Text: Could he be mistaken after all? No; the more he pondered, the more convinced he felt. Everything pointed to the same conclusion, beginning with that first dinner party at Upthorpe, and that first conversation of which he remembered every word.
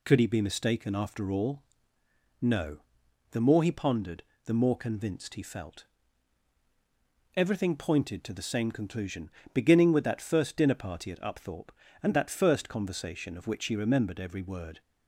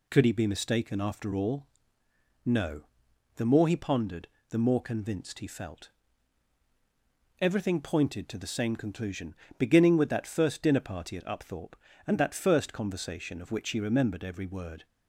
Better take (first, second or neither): neither